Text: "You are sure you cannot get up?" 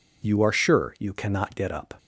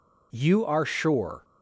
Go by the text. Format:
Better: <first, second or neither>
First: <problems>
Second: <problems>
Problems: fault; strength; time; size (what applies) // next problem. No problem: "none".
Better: first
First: none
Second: stops before "you cannot get up"; at 1.4 s